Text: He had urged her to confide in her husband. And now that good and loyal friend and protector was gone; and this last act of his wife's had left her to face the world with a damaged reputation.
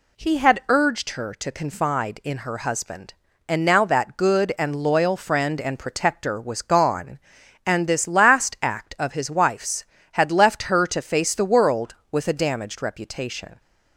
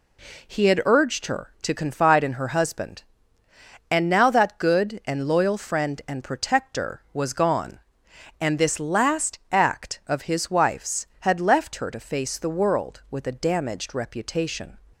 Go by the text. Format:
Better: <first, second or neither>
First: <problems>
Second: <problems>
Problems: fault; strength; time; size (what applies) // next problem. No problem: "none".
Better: neither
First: none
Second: none